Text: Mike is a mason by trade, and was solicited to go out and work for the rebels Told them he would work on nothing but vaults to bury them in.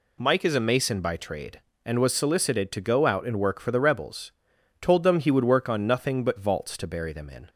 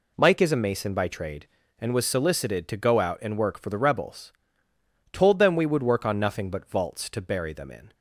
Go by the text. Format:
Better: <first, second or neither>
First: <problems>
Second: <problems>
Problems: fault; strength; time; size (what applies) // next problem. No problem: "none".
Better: first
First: pauses between "rebels" and "Told"; noticeable; at 4.3 s; 0.48 s long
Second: pauses between "rebels" and "Told"; noticeable; at 4.3 s; 0.80 s long // says "we" for "he"; at 5.5 s